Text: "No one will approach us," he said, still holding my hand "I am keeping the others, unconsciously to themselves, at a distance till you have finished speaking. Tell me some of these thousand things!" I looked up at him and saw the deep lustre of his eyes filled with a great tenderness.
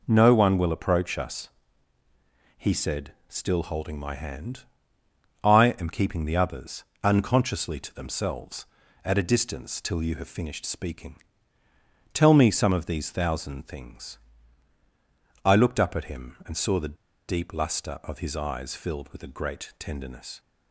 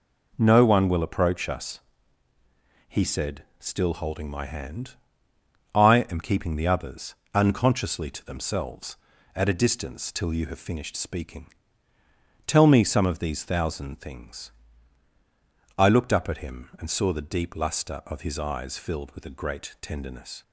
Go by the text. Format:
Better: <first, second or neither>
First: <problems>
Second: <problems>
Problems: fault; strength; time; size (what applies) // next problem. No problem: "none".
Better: second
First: pauses between "hand" and "I"; noticeable; at 4.6 s; 0.78 s long // pauses between "the" and "deep"; slight; at 16.9 s; 0.30 s long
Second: pauses between "hand" and "I"; noticeable; at 4.9 s; 0.78 s long